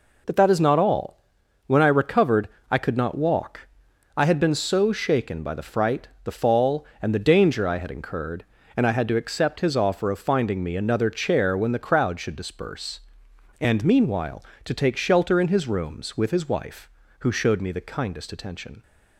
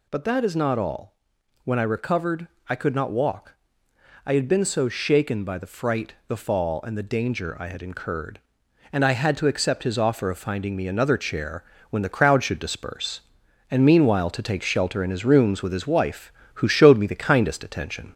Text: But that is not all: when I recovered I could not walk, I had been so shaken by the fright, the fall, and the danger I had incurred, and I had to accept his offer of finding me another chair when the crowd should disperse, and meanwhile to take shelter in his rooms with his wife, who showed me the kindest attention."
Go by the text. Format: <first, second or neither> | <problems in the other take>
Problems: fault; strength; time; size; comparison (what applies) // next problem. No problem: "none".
first | gets louder; slight; throughout; 2.5 dB // pauses between "recovered" and "I"; slight; at 2.4 s; 0.22 s long; slight in the first // pauses between "chair" and "when"; slight; at 11.6 s; 0.26 s long